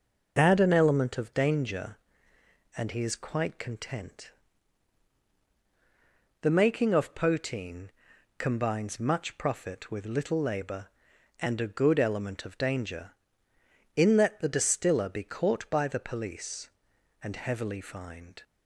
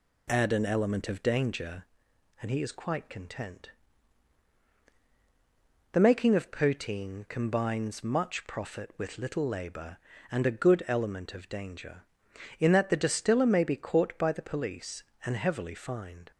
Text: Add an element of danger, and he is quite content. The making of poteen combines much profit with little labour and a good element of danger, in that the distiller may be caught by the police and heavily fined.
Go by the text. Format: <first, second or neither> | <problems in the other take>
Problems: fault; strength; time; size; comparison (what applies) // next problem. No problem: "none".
second | pauses between "poteen" and "combines"; noticeable; at 7.8 s; 0.48 s long // skips "may"; at 15.0 s